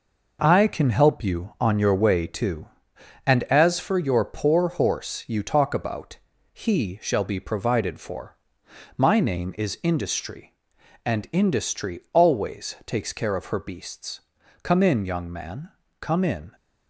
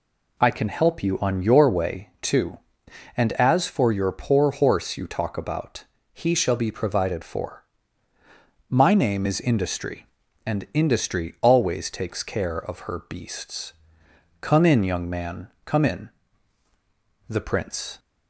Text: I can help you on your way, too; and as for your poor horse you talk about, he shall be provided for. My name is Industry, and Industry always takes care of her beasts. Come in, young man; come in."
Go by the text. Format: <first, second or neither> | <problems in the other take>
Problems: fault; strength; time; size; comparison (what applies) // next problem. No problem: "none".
first | goes on to say "The Prince"; noticeable; from 17.2 s on; 0.70 s long